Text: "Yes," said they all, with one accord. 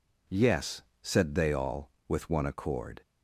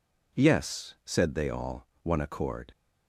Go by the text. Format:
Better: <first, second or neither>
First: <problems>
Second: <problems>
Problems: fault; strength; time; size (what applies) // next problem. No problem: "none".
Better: first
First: none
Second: skips "with"; at 1.9 s